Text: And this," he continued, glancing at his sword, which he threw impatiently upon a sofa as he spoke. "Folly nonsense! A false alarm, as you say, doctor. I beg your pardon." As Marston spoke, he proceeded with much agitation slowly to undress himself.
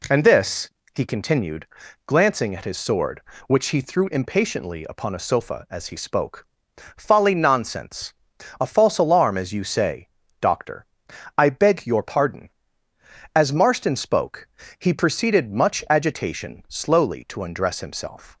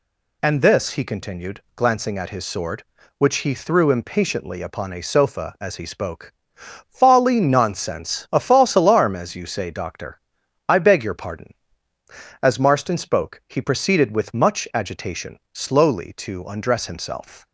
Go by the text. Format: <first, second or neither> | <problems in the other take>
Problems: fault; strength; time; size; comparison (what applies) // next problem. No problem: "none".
second | skips "with"; at 15.5 s